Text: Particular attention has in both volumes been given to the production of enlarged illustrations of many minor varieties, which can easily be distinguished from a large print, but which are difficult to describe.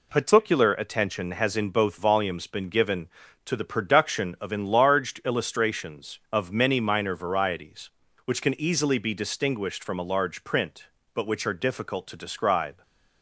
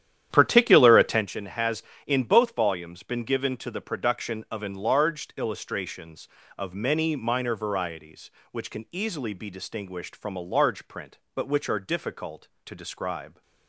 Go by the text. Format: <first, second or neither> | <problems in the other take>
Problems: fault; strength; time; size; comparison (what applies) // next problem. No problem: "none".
first | starts louder than the rest; strong; until 1.3 s; 10.5 dB